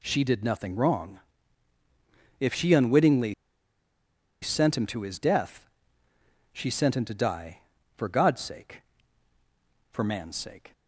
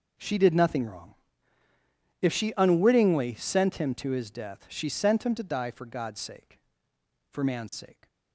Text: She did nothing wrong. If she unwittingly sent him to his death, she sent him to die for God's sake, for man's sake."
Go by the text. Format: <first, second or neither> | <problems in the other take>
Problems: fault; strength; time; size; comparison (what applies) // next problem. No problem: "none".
second | pauses between "unwittingly" and "sent"; at 3.3 s; 1.0 s long